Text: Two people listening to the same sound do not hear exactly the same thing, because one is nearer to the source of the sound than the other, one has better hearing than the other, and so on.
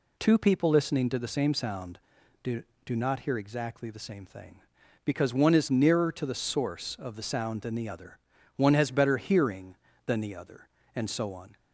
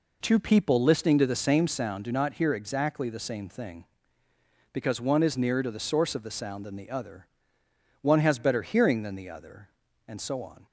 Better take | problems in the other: second | says "do" twice; at 2.8 s

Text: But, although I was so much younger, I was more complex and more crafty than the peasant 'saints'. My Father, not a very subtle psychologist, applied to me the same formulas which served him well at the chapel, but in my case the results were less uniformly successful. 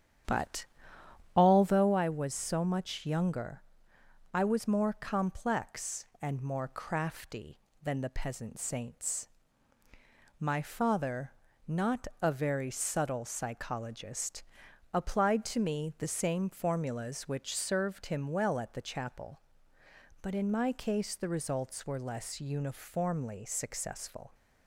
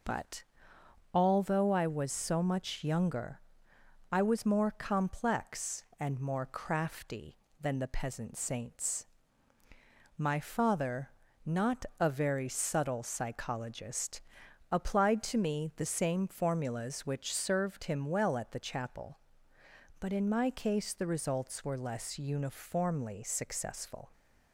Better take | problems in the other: second | starts louder than the rest; strong; until 2.0 s; 9.5 dB

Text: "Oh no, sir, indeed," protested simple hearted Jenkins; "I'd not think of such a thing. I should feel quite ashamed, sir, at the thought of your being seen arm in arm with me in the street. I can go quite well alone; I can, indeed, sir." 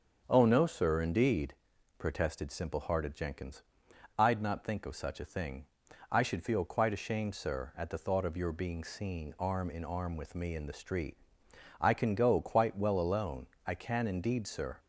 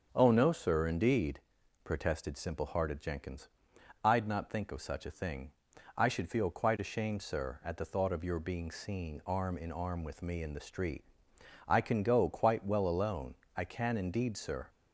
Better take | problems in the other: neither | starts louder than the rest; the same in both

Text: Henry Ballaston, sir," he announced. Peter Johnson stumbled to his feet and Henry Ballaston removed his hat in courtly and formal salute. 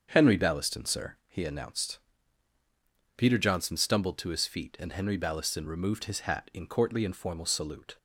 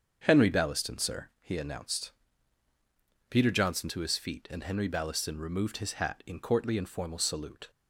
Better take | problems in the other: first | starts louder than the rest; until 1.2 s; 7 dB; also in the first // skips "stumbled"; at 3.8 s

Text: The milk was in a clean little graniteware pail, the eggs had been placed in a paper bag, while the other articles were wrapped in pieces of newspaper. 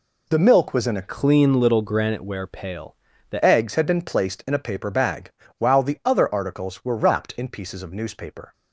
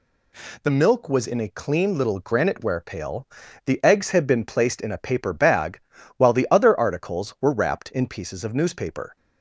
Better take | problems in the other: second | changes voice from "clean" to "the"; from 1.0 to 3.4 s; 2.4 s long

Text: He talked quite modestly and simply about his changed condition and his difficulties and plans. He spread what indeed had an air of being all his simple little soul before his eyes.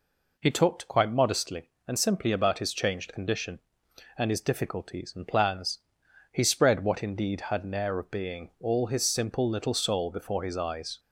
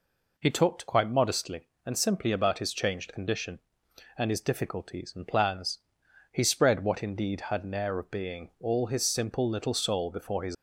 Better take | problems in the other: first | stops before "eyes"; at 10.5 s

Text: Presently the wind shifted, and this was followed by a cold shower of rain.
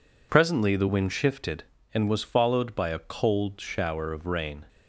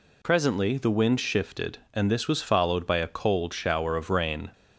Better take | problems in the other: second | skips "this"; at 2.0 s

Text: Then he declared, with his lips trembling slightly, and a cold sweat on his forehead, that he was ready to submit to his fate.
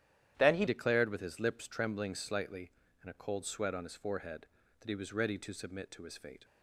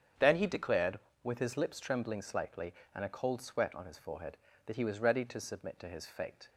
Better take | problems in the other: second | starts louder than the rest; strong; until 1.3 s; 11 dB; strong in the second // changes voice at "declared"; from 0.6 s on; 5.8 s long

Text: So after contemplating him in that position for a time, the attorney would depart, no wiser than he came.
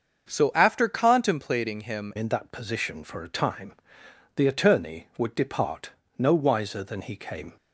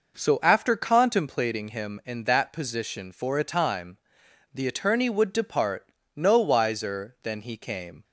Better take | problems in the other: second | starts louder than the rest; until 1.3 s; 6.5 dB // changes voice at "in"; from 2.1 s on; 5.4 s long

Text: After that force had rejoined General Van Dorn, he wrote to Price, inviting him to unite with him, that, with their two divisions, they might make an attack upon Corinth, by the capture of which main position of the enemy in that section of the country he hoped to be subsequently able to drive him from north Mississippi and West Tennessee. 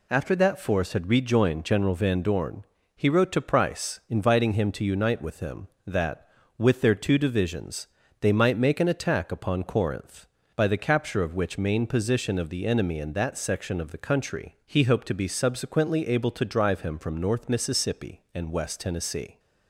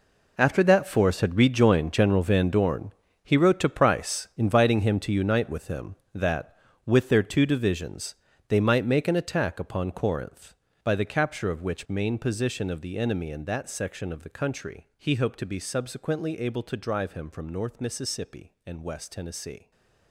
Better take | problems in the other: first | gets quieter; strong; throughout; 14.5 dB // stays silent after the last word; slight; from 19.5 s on; 0.5 s long

